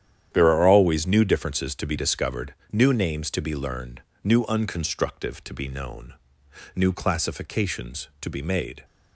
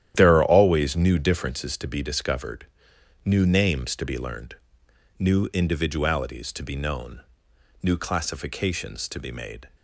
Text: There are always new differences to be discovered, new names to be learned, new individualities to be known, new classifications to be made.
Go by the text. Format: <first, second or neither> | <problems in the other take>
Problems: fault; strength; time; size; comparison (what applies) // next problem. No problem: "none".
second | starts louder than the rest; strong; until 1.3 s; 10 dB; strong in the second // says "unconstructive" for "individualities"; at 4.4 s